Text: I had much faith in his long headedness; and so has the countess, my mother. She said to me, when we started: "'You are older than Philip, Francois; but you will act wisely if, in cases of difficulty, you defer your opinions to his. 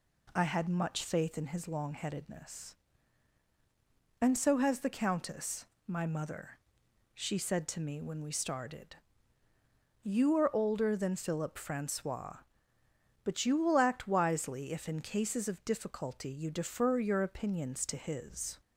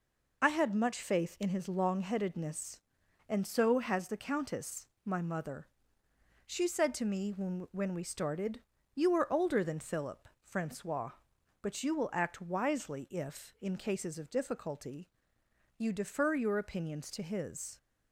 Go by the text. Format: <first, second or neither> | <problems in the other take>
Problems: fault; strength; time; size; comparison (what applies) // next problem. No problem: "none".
first | says "when" twice; at 7.7 s